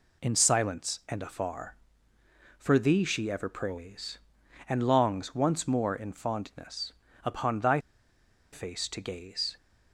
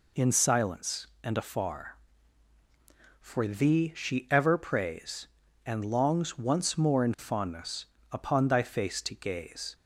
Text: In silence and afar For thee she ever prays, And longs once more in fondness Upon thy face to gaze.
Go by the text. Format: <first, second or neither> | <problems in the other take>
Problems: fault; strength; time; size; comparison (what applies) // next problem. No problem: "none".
second | pauses between "fondness" and "Upon"; slight; at 6.9 s; 0.30 s long; slight in the second // pauses between "thy" and "face"; noticeable; at 7.7 s; 0.74 s long